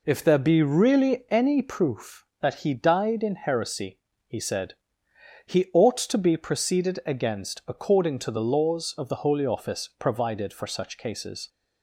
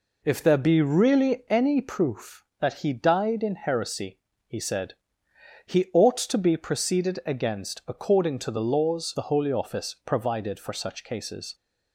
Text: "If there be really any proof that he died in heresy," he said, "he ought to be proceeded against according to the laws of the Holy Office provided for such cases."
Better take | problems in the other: first | skips "of"; at 9.1 s

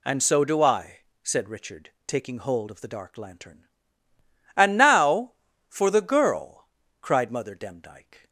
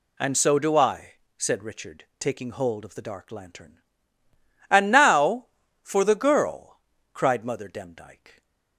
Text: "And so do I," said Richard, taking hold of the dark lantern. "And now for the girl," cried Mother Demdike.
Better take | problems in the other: neither | none

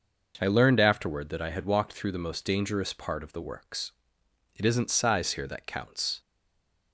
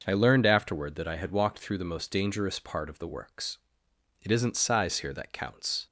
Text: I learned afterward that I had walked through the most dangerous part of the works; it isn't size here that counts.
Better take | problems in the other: second | stays silent after the last word; slight; from 6.1 s on; 0.8 s long

